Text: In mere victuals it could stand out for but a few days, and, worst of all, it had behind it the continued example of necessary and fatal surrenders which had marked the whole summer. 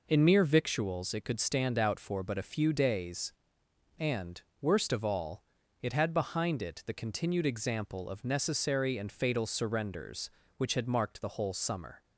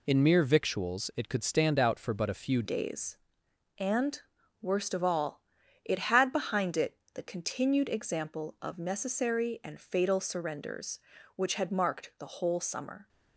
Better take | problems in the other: first | changes voice at "days"; from 2.6 s on; 10.4 s long // pauses between "it" and "the"; slight; at 6.9 s; 0.18 s long

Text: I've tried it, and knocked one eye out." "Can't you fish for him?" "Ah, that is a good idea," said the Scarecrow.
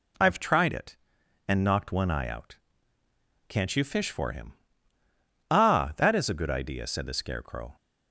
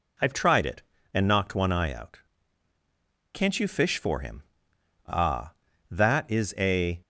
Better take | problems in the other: first | stops before "good idea said the Scarecrow"; at 7.0 s

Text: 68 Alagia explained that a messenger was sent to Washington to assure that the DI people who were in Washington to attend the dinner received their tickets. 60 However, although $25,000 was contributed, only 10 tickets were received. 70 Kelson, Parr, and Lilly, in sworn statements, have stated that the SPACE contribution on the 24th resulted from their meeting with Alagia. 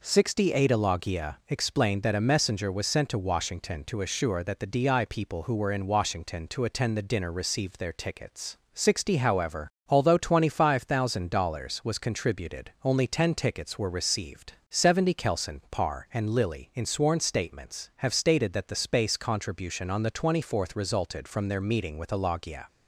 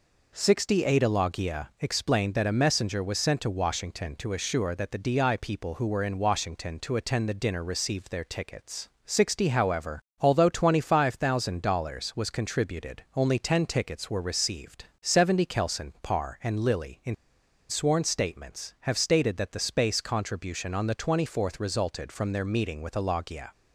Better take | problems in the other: first | pauses between "in" and "sworn"; noticeable; at 17.1 s; 0.54 s long

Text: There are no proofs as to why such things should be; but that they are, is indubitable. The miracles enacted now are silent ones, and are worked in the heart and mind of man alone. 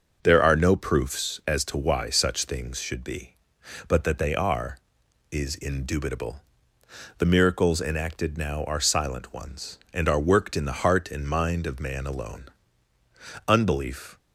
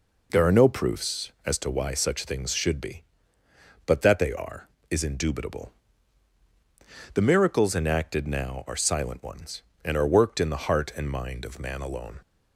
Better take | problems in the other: second | starts louder than the rest; noticeable; until 1.2 s; 6 dB // goes on to say "Unbelief"; noticeable; from 13.4 s on; 0.70 s long

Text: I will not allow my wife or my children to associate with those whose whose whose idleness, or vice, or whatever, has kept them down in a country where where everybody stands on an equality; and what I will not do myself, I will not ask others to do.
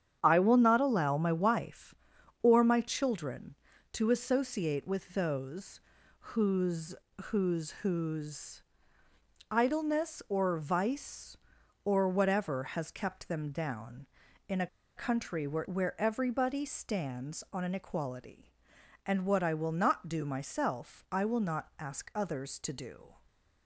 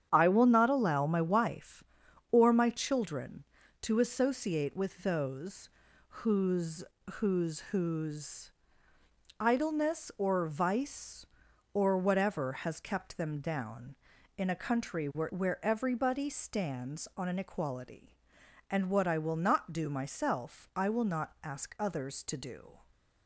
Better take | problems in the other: second | starts louder than the rest; strong; until 1.2 s; 8.5 dB; strong in the second // pauses between "those" and "whose"; at 5.8 s; 0.38 s long; also in the second // pauses between "whose" and "whose"; slight; at 6.9 s; 0.32 s long; slight in the second // pauses between "whose" and "idleness"; noticeable; at 8.6 s; 0.88 s long; noticeable in the second // pauses between "a" and "country"; slight; at 14.6 s; 0.30 s long

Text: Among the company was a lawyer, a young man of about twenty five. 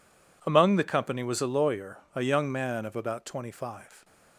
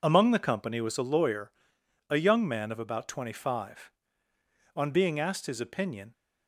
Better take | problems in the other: first | goes on to say "On being asked his opinion"; from 4.7 s on; 1.3 s long

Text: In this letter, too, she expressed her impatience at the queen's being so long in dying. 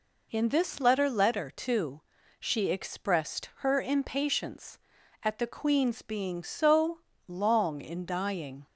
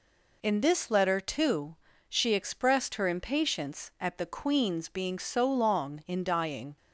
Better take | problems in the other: second | says "letter" twice; at 1.0 s // pauses between "so" and "long"; slight; at 6.9 s; 0.26 s long

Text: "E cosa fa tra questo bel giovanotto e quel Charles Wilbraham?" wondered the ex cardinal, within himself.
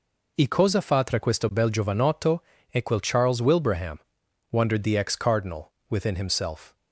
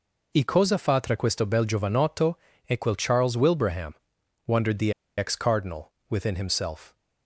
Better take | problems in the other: first | pauses between "giovanotto" and "e"; slight; at 2.3 s; 0.26 s long; slight in the first // pauses between "the" and "ex"; slight; at 4.9 s; 0.25 s long

